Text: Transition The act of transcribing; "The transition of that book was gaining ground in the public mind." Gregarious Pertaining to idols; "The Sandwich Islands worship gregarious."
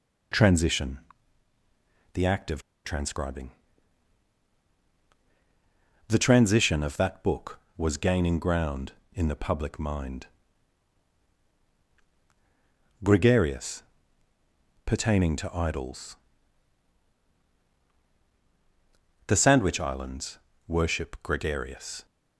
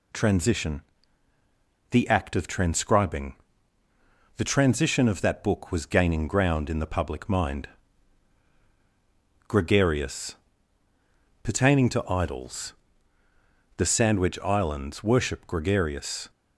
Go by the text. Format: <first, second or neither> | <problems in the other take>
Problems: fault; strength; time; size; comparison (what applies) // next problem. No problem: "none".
second | pauses between "Transition" and "The"; at 0.9 s; 1.1 s long; also in the second // pauses between "of" and "transcribing"; slight; at 2.6 s; 0.23 s long // pauses between "Gregarious" and "Pertaining"; at 13.8 s; 1.0 s long; also in the second // pauses between "Islands" and "worship"; slight; at 20.3 s; 0.30 s long